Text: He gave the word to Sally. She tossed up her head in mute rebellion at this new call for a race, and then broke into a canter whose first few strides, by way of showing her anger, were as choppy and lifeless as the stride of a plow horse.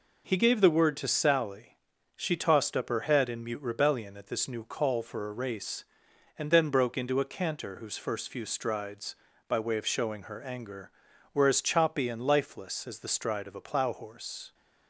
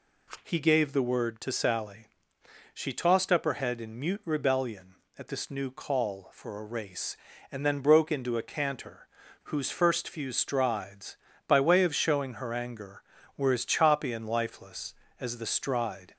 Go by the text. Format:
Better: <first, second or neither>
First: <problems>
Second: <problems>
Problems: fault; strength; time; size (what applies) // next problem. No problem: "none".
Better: first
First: none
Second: pauses between "canter" and "whose"; at 9.0 s; 0.38 s long // stops before "of a plow horse"; at 16.1 s